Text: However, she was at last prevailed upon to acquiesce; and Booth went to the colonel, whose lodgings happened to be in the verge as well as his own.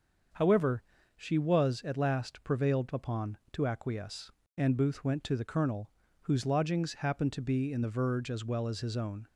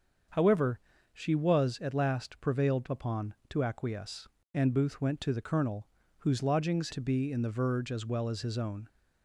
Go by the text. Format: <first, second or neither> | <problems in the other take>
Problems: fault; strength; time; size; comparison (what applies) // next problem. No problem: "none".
first | starts louder than the rest; until 1.6 s; 7 dB; also in the first // skips "happened"; at 6.9 s